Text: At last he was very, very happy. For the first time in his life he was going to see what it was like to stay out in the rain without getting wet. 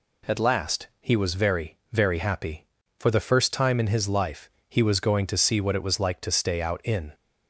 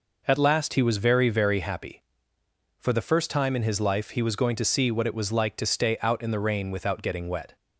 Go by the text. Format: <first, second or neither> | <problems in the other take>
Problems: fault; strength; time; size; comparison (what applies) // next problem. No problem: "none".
second | pauses between "life" and "he"; slight; at 4.4 s; 0.20 s long // stops before "the rain without getting wet"; at 7.1 s